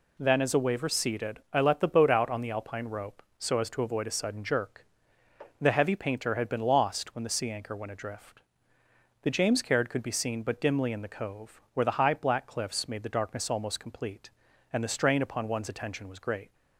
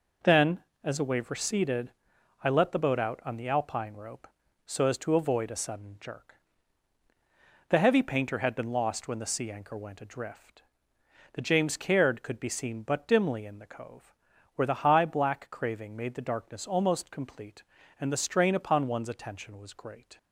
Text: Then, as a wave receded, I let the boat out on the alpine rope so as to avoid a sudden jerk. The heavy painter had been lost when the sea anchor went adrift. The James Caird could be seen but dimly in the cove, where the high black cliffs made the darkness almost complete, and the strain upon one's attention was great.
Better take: first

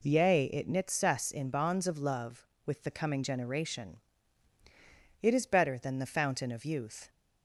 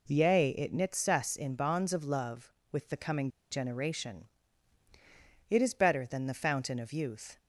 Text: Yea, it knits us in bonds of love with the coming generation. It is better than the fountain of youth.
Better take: first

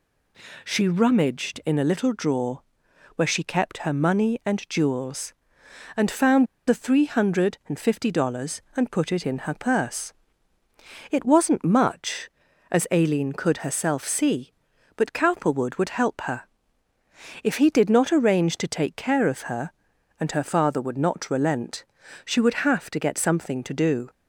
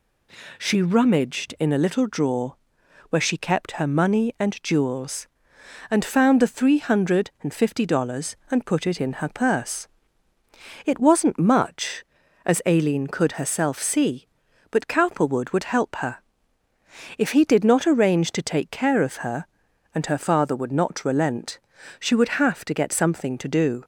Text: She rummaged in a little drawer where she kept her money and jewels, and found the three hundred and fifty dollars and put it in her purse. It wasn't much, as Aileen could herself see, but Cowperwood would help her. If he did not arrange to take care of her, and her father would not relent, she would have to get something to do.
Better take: second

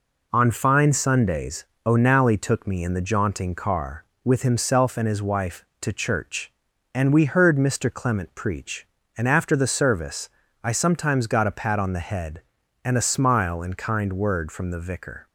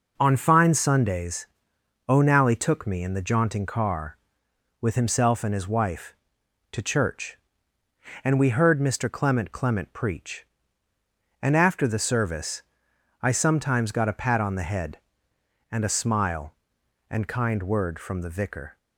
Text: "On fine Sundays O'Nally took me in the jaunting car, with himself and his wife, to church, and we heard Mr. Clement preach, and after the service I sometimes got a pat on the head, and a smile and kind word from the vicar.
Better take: first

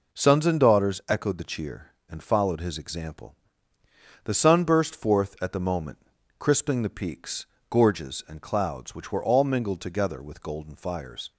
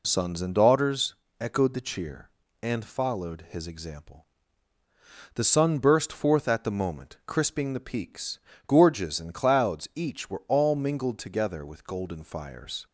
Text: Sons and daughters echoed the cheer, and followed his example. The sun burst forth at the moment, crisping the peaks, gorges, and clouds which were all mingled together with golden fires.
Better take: first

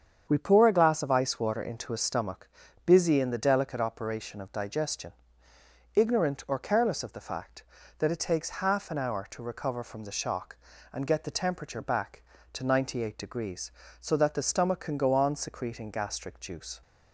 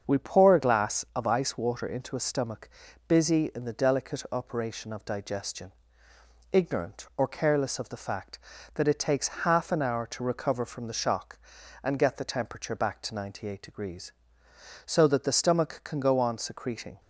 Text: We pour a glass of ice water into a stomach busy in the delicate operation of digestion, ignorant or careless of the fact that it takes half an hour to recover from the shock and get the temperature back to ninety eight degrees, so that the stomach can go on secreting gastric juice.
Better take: first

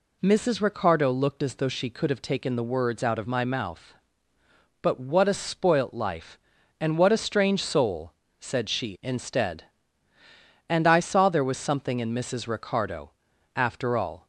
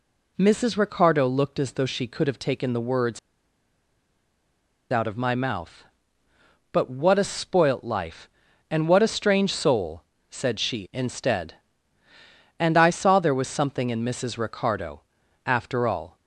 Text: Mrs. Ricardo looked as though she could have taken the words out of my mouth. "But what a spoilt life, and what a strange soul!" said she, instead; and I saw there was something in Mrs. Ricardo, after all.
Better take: first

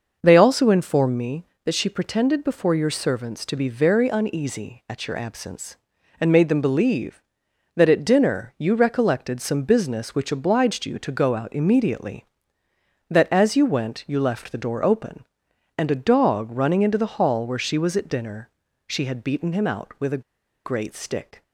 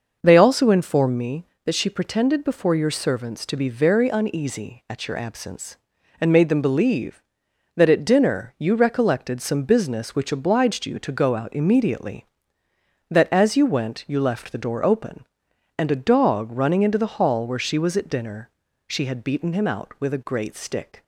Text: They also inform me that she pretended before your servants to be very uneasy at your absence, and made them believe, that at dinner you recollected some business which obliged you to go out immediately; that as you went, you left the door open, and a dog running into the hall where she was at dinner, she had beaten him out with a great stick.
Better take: second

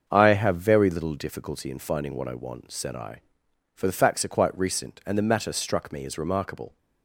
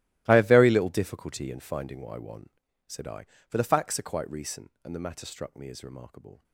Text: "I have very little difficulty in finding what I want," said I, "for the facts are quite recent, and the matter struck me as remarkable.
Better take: first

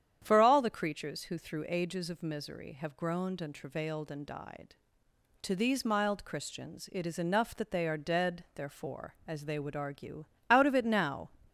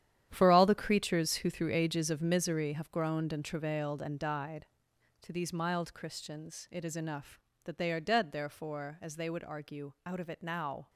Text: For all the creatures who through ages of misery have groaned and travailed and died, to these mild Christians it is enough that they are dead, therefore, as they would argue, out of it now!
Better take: first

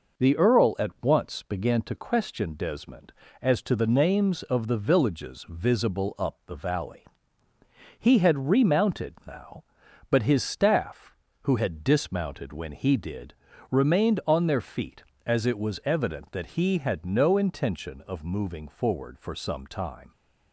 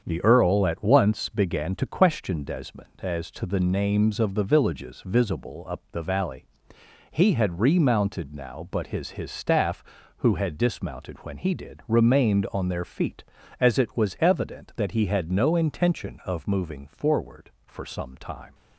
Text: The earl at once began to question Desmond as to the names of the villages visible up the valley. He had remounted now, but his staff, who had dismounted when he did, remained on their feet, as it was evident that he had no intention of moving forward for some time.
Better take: first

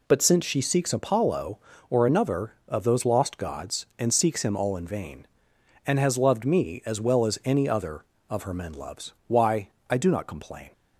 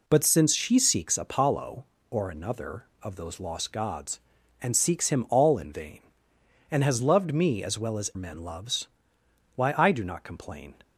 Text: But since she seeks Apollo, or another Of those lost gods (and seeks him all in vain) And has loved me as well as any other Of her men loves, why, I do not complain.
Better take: first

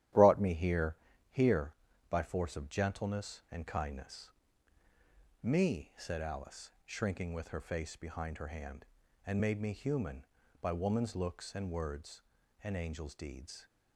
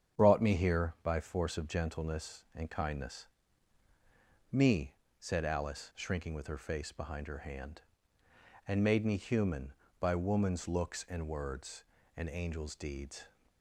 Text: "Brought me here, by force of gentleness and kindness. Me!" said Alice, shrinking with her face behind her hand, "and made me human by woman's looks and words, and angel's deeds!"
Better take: second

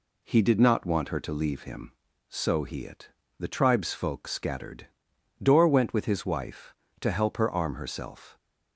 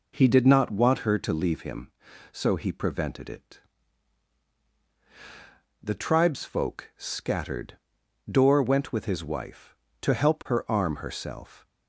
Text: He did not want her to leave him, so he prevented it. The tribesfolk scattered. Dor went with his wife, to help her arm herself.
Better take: second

